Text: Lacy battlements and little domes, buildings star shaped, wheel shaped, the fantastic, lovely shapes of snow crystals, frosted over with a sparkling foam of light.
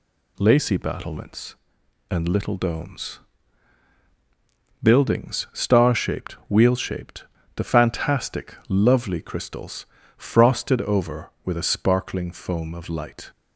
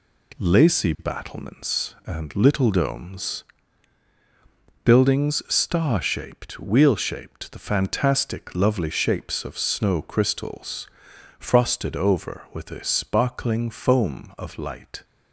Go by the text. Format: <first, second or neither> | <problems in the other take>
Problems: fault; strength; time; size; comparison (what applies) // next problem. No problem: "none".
second | skips "shapes of snow"; at 9.2 s